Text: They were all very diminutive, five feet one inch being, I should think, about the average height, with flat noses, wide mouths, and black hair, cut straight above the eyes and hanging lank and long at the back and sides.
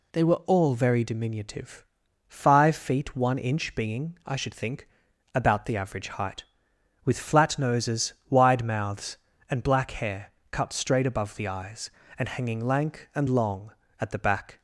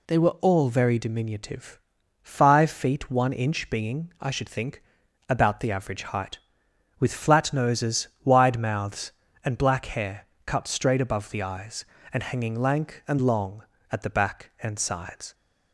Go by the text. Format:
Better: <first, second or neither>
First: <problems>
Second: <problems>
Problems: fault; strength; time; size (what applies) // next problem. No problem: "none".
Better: second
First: stops before "and sides"; at 14.5 s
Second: none